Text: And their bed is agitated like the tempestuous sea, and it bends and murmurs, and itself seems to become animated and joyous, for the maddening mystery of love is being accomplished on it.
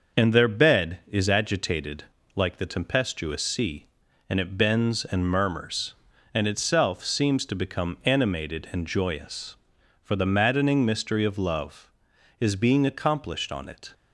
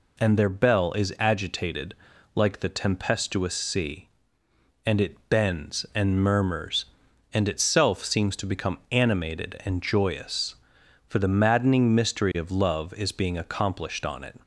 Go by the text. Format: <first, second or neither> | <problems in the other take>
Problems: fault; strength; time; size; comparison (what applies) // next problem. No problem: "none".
first | says "bell" for "bed"; at 0.4 s // pauses between "agitated" and "like"; at 1.9 s; 0.40 s long; slight in the first